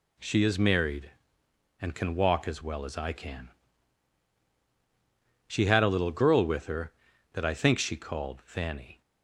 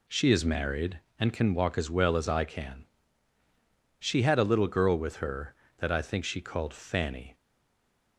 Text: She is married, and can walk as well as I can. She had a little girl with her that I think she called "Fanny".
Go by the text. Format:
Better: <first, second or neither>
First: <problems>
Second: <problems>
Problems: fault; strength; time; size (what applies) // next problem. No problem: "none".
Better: first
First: none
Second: stays silent after the last word; slight; from 7.3 s on; 0.8 s long